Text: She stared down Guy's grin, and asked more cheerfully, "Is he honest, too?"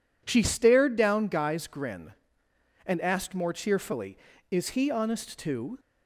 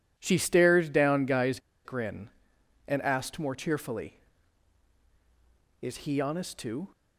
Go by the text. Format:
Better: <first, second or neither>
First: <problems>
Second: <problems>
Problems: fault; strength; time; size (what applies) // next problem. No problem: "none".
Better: first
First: none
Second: pauses between "Guy's" and "grin"; slight; at 1.5 s; 0.26 s long